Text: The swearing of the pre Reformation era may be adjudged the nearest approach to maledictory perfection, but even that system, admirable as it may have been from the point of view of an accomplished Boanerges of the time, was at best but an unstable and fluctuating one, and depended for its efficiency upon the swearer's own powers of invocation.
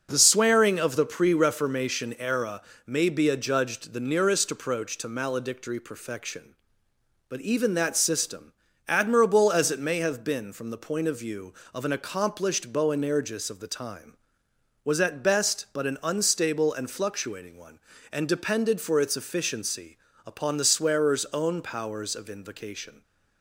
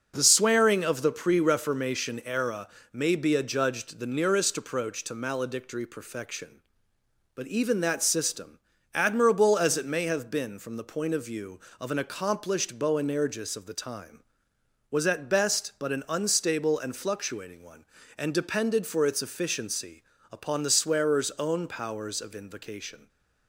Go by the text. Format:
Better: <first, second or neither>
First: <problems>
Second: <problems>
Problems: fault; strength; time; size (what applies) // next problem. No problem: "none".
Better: neither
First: starts louder than the rest; until 1.1 s; 6 dB // pauses between "era" and "may"; slight; at 2.6 s; 0.24 s long // pauses between "efficiency" and "upon"; slight; at 19.9 s; 0.26 s long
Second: starts louder than the rest; until 1.1 s; 6 dB // pauses between "era" and "may"; slight; at 2.6 s; 0.24 s long // pauses between "efficiency" and "upon"; slight; at 20.0 s; 0.26 s long